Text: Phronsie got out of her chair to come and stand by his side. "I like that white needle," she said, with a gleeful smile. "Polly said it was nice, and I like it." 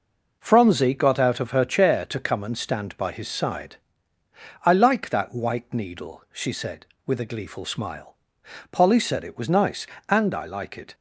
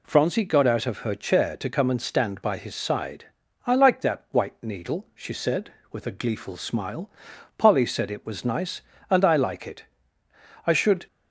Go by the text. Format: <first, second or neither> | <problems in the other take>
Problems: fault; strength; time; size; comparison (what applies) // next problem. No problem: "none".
first | goes on to say "I should"; slight; from 10.6 s on; 0.40 s long